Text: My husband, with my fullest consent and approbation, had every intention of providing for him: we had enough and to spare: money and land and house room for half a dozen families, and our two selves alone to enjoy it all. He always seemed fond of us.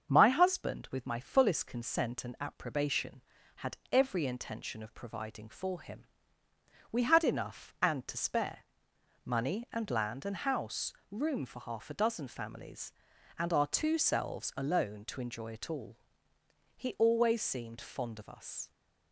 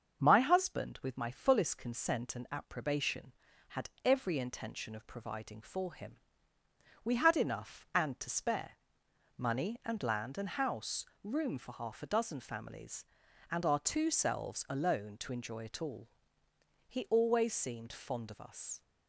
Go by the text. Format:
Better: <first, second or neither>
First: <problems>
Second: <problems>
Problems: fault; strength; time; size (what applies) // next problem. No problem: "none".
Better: neither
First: starts louder than the rest; until 1.1 s; 7 dB // pauses between "had" and "every"; slight; at 3.7 s; 0.16 s long // pauses between "house" and "room"; slight; at 10.9 s; 0.16 s long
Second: starts louder than the rest; until 1.2 s; 7 dB // pauses between "had" and "every"; slight; at 3.8 s; 0.16 s long // pauses between "house" and "room"; slight; at 11.0 s; 0.16 s long